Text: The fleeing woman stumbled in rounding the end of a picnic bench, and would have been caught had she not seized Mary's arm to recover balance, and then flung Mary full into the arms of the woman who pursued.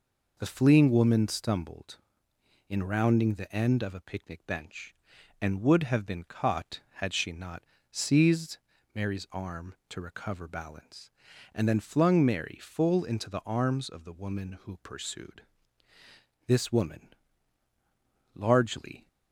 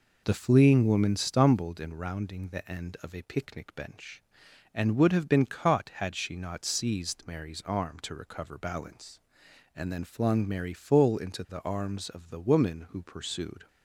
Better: second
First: pauses between "not" and "seized"; slight; at 7.6 s; 0.28 s long // pauses between "seized" and "Mary's"; slight; at 8.5 s; 0.36 s long // goes on to say "This woman largely"; strong; from 16.4 s on; 2.6 s long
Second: none

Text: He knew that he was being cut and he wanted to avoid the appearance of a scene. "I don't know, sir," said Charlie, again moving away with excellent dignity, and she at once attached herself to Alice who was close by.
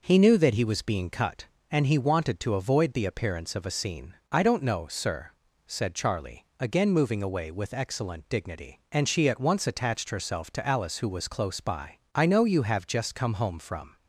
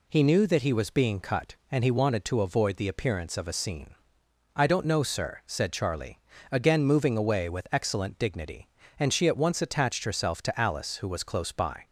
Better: second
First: goes on to say "I know you have just come home from"; strong; from 12.1 s on; 1.8 s long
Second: none

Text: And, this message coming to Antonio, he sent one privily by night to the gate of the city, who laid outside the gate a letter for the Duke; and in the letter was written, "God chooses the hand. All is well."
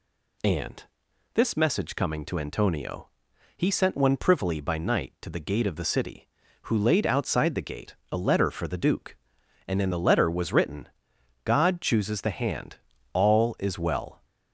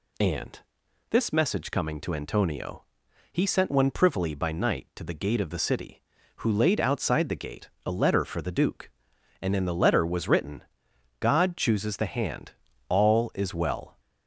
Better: neither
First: pauses between "gate" and "a"; slight; at 7.9 s; 0.18 s long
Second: pauses between "gate" and "a"; slight; at 7.6 s; 0.18 s long

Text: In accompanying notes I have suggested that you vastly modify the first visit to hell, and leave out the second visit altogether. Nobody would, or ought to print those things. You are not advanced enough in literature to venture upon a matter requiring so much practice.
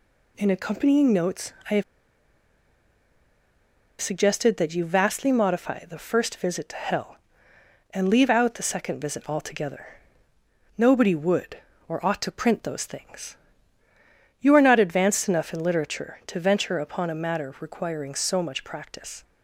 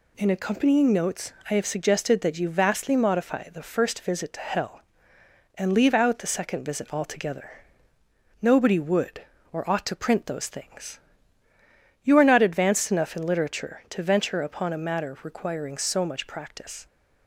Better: second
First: pauses between "notes" and "I"; slight; at 1.5 s; 0.18 s long // pauses between "have" and "suggested"; strong; at 1.8 s; 2.1 s long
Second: pauses between "notes" and "I"; slight; at 1.3 s; 0.18 s long

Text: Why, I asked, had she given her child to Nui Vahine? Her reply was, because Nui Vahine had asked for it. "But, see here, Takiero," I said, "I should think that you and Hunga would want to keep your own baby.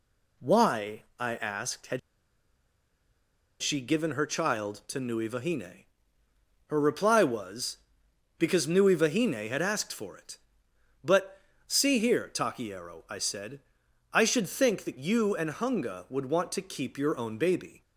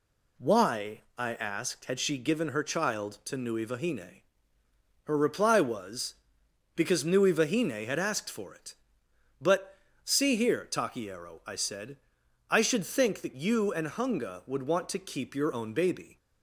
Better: second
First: pauses between "had" and "she"; strong; at 1.9 s; 1.6 s long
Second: none

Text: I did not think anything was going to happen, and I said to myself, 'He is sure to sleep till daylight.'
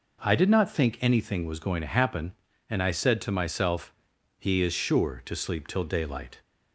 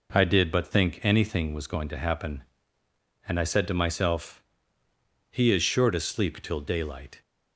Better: first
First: none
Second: says "but" for "not"; at 0.5 s

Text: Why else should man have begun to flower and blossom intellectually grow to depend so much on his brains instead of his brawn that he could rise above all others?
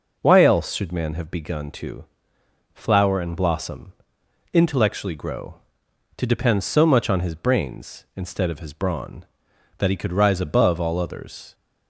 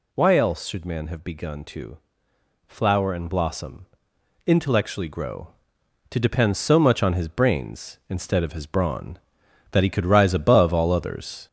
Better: first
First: pauses between "to" and "flower"; noticeable; at 2.0 s; 0.70 s long // pauses between "blossom" and "intellectually"; noticeable; at 3.9 s; 0.60 s long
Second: gets louder; noticeable; throughout; 4.5 dB // pauses between "to" and "flower"; noticeable; at 1.9 s; 0.70 s long // pauses between "blossom" and "intellectually"; noticeable; at 3.8 s; 0.60 s long

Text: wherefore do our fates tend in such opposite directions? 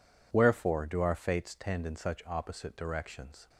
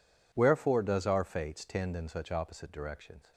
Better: first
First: none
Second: says "does" for "do"; at 0.8 s

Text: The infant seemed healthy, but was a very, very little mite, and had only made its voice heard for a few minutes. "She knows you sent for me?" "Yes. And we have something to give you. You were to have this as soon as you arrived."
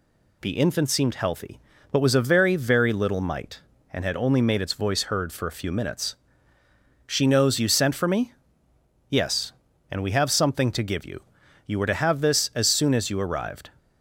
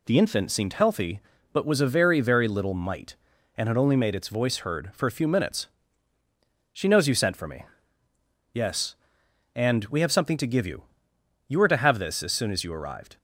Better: neither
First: none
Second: none

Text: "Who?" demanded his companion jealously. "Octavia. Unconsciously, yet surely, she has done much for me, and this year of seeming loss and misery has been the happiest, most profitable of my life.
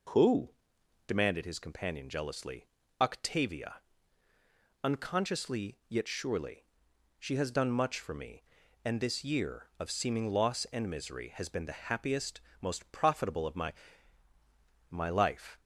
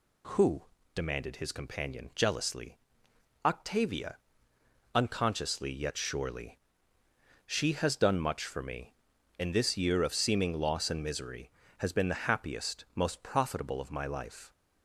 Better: second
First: says "my" twice; at 14.8 s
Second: none

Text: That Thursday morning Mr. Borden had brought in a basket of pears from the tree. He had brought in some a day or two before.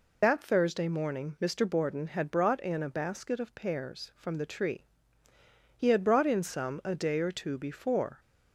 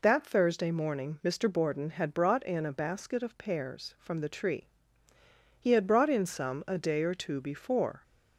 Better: second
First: loses the start of "That"; at 0.2 s; 25 ms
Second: none

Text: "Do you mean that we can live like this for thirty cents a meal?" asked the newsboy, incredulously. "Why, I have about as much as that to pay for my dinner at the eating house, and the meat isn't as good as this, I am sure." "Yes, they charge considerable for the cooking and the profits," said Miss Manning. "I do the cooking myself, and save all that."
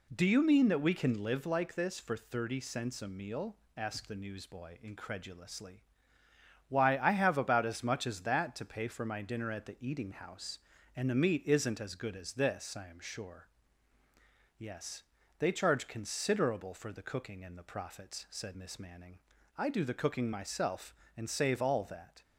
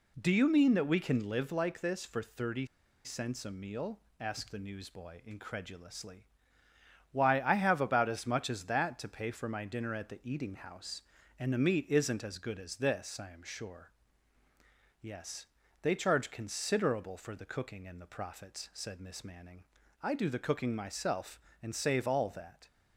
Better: first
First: none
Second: pauses between "thirty" and "cents"; at 2.6 s; 0.38 s long

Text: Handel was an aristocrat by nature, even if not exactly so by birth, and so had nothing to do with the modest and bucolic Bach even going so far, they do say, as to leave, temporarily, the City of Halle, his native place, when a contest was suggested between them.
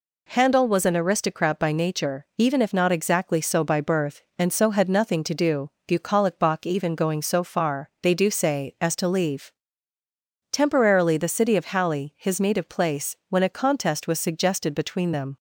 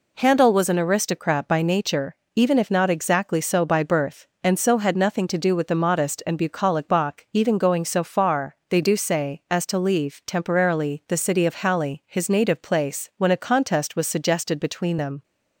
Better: second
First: skips "with the modest and"; at 5.7 s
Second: none

